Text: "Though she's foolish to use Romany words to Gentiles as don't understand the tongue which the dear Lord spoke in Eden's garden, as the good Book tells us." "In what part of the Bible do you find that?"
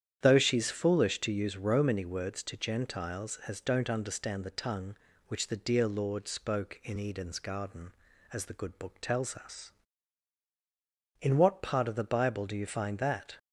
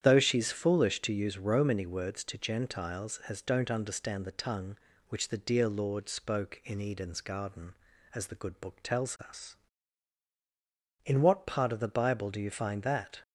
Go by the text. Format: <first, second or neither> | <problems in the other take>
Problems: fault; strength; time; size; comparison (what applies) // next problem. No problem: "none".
neither | starts louder than the rest; strong; the same in both